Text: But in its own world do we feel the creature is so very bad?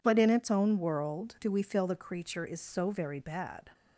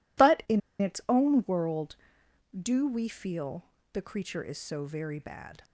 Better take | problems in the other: first | pauses between "in" and "its"; slight; at 0.6 s; 0.19 s long // pauses between "feel" and "the"; slight; at 3.6 s; 0.26 s long

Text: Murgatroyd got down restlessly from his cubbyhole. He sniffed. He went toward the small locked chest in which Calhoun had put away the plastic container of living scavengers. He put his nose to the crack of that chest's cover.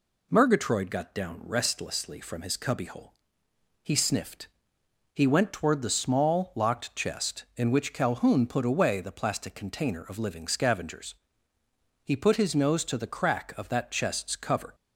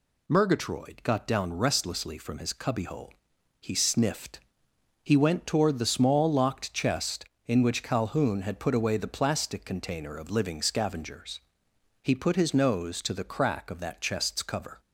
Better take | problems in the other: second | skips "had"; at 8.4 s

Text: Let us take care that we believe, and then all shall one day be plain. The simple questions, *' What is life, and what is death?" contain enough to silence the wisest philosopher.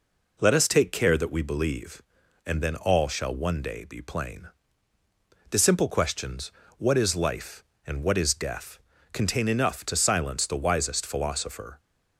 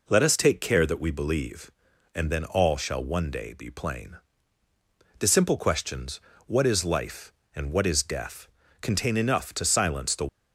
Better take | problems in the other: first | stops before "wisest philosopher"; at 10.2 s

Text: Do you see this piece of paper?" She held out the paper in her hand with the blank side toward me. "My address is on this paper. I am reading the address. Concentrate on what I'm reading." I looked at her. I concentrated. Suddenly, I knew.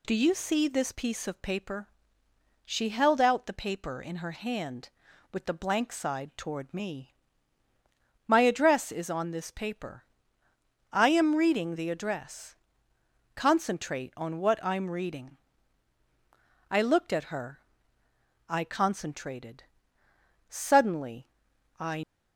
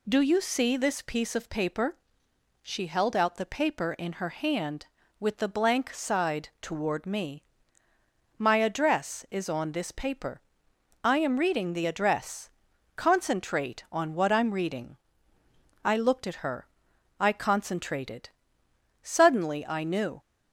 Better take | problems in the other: second | stops before "knew"; at 22.0 s

